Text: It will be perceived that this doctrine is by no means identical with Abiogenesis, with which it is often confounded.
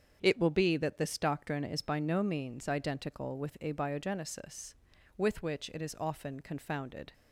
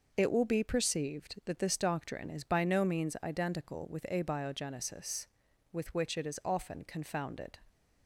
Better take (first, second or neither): second